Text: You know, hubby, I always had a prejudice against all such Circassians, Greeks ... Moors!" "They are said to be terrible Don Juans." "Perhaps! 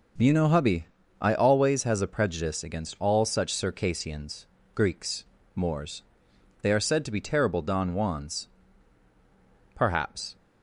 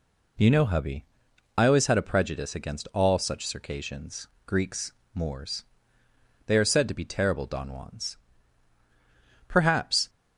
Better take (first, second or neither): second